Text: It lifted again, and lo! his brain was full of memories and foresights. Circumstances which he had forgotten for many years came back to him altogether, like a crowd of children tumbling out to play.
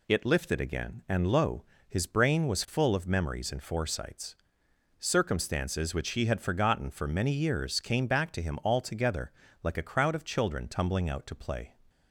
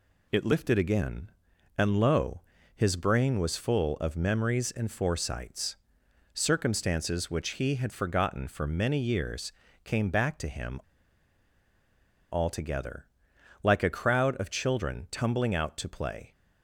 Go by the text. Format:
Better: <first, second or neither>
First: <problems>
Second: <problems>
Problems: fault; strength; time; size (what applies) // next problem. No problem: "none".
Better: first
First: none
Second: pauses between "years" and "came"; slight; at 9.5 s; 0.32 s long // pauses between "him" and "altogether"; strong; at 10.8 s; 1.5 s long